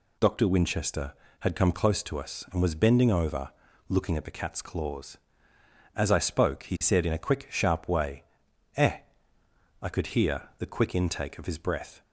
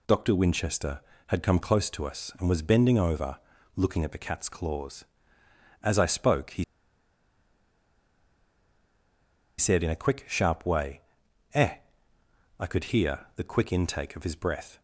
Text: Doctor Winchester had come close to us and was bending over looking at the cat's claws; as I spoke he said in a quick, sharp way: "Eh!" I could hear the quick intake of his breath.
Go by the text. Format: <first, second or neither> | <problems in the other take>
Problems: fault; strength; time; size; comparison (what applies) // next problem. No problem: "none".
first | pauses between "over" and "looking"; slight; at 3.3 s; 0.36 s long; slight in the first // pauses between "he" and "said"; strong; at 6.6 s; 2.9 s long